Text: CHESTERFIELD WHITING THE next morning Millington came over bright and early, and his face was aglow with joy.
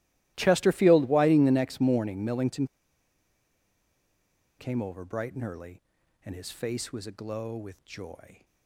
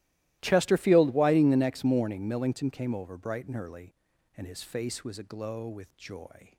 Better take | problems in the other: second | starts louder than the rest; strong; until 1.3 s; 17 dB; strong in the second // pauses between "Millington" and "came"; strong; at 2.6 s; 1.9 s long

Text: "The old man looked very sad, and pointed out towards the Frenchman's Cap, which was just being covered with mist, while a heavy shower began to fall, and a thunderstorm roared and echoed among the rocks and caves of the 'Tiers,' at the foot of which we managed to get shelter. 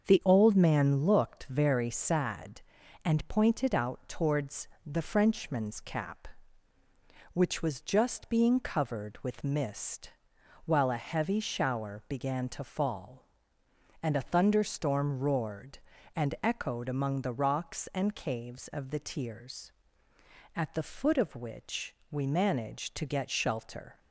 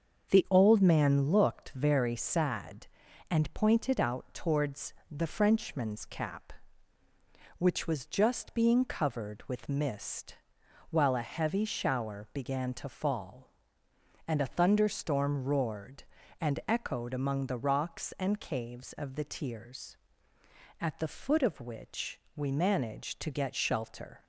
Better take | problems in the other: neither | starts louder than the rest; the same in both // pauses between "towards" and "the"; slight; the same in both // pauses between "which" and "we"; slight; the same in both

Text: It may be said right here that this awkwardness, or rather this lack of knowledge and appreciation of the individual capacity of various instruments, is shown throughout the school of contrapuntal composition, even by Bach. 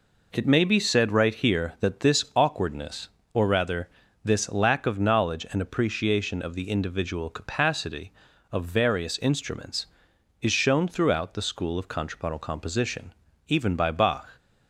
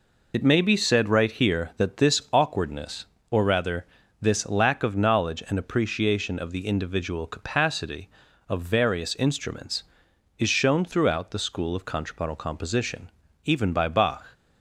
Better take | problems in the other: first | loses the start of "It"; at 0.3 s; 50 ms // pauses between "rather" and "this"; slight; at 3.8 s; 0.34 s long; slight in the first

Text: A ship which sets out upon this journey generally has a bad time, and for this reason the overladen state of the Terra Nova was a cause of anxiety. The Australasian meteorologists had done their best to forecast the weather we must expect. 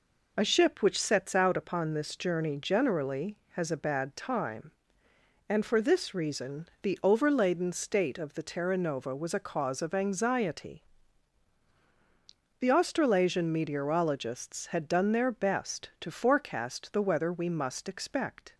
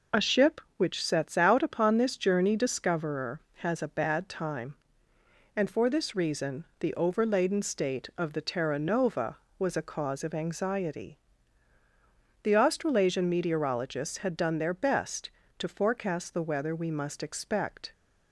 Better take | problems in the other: first | says "discoverer" for "generally"; at 2.5 s // pauses between "reason" and "the"; slight; at 6.6 s; 0.16 s long

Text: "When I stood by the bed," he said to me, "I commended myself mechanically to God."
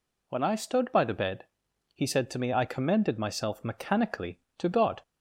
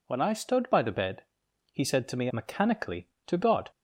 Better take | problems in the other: first | skips "I commended myself"; at 2.2 s

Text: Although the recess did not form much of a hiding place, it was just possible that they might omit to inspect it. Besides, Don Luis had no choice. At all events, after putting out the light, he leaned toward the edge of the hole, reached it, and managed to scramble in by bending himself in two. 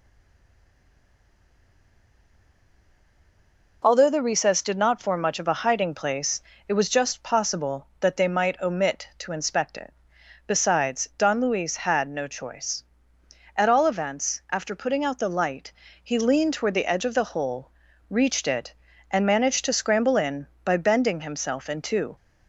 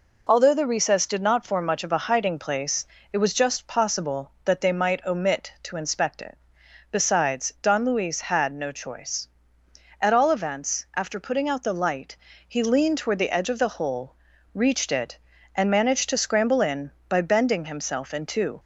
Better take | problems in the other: second | stays silent before the first word; strong; until 3.8 s; 3.8 s long

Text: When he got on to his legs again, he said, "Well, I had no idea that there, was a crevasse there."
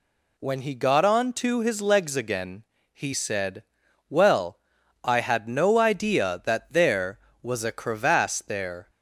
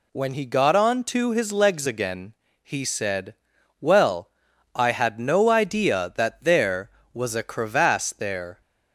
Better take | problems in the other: neither | none

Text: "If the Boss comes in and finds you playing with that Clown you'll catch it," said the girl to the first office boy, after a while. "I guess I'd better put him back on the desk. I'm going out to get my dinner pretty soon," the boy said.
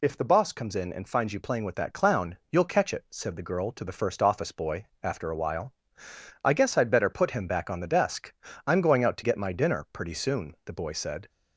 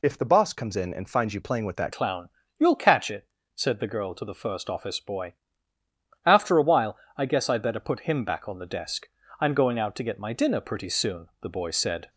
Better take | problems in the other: first | changes voice at "Clown"; from 1.9 s on; 10.1 s long // pauses between "Clown" and "you'll"; slight; at 2.2 s; 0.32 s long; slight in the first

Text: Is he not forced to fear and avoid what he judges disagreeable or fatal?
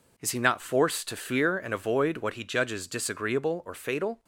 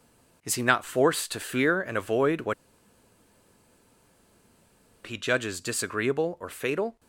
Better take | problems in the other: first | pauses between "what" and "he"; strong; at 2.5 s; 2.5 s long

